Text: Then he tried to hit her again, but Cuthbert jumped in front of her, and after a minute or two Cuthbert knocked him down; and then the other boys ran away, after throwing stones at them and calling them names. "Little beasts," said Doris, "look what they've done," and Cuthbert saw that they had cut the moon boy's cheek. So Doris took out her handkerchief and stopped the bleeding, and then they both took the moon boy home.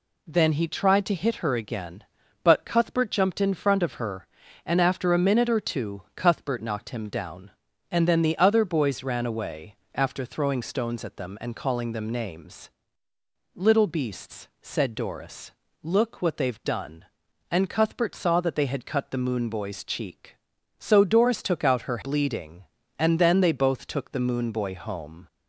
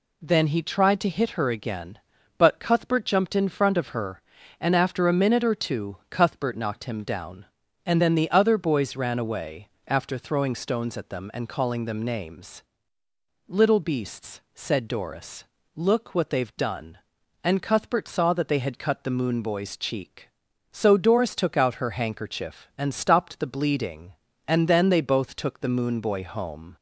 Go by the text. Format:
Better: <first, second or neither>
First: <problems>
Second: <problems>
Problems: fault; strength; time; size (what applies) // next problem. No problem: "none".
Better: second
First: skips "handkerchief and stopped the"; at 22.0 s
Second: none